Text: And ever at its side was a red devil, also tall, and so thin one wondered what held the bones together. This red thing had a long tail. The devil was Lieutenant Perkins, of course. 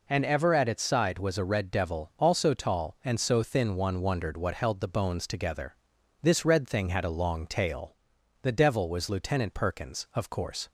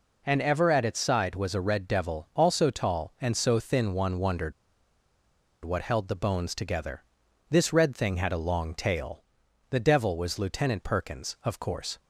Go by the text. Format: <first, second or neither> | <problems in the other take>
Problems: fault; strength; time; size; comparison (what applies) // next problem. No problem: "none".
first | pauses between "wondered" and "what"; at 4.5 s; 1.1 s long